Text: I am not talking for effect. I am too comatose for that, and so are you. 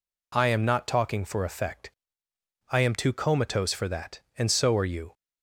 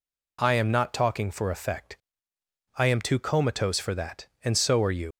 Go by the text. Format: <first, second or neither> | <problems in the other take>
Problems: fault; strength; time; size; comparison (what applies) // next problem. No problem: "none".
first | leaves "you" unfinished; at 5.1 s; 85 ms